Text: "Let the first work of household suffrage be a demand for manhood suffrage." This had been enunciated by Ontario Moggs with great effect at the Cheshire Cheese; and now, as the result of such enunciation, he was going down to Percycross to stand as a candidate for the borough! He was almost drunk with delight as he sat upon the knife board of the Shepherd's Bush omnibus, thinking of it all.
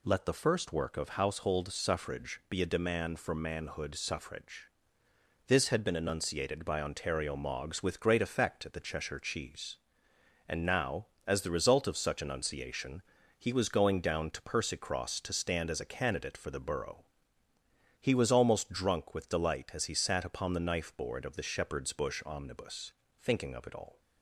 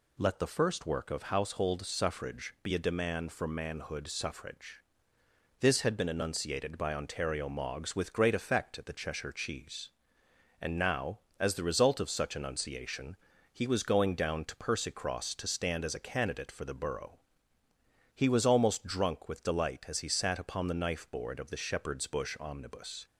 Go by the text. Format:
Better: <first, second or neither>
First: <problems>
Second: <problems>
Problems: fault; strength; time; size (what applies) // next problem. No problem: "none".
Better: first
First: none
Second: stops before "thinking of it all"; at 23.0 s